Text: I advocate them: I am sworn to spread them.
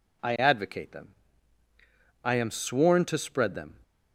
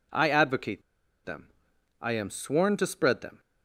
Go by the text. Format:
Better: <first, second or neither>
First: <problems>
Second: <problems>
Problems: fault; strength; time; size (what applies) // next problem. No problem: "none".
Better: first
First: none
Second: pauses between "advocate" and "them"; at 0.8 s; 0.43 s long